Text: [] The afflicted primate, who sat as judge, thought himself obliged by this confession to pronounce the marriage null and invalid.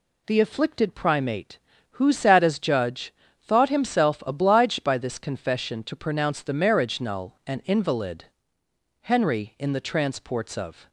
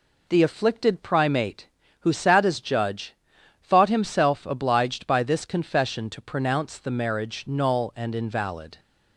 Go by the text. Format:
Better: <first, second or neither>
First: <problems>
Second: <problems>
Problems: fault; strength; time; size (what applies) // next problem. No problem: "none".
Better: second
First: goes on to say "Henry in the transports of"; strong; from 9.0 s on; 1.8 s long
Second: none